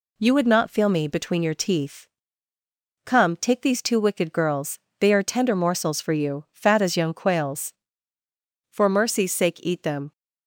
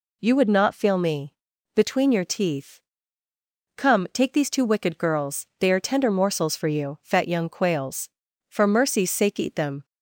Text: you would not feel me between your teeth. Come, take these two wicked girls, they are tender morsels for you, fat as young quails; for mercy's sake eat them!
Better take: first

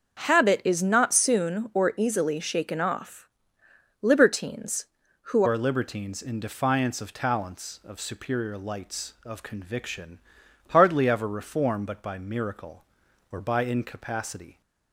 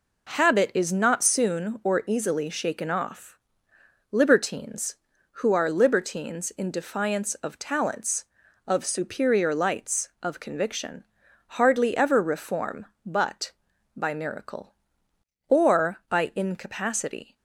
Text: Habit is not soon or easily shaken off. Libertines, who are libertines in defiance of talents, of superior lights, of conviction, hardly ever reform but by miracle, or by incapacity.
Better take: second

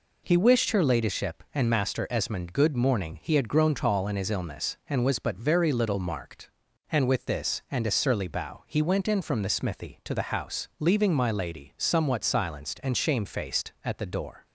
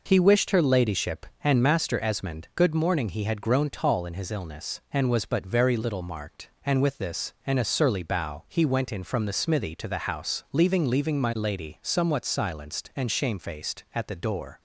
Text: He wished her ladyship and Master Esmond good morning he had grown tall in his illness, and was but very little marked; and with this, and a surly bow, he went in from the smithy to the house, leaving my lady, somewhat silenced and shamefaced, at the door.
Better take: first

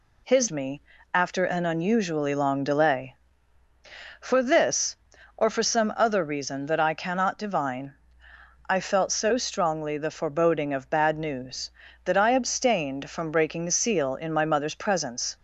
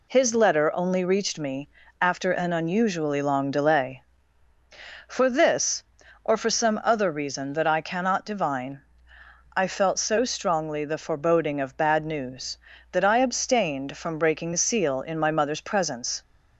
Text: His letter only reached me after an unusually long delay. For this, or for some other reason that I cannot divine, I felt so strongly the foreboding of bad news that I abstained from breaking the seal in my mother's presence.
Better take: second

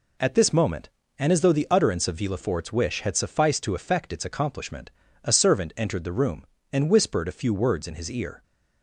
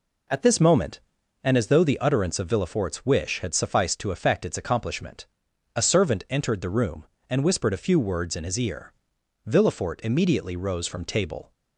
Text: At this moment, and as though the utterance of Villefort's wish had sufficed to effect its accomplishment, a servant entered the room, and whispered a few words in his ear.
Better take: first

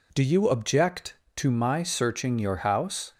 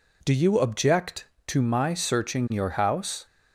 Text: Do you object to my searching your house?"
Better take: neither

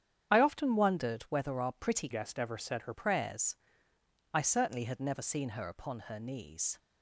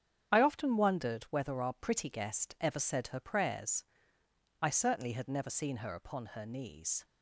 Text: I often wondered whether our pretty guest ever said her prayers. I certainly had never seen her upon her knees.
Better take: second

